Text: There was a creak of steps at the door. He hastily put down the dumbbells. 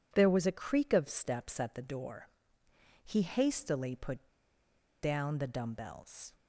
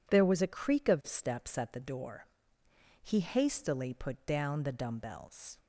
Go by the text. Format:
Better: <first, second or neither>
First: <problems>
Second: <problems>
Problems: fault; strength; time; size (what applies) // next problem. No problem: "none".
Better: second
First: pauses between "put" and "down"; noticeable; at 4.2 s; 0.76 s long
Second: none